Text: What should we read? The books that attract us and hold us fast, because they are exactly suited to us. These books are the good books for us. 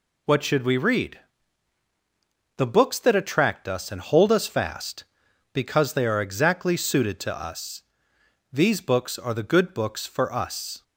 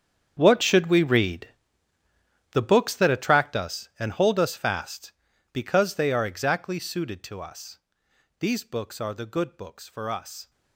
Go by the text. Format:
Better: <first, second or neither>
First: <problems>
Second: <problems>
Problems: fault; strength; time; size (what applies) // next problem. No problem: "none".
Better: first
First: none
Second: gets quieter; strong; throughout; 16.5 dB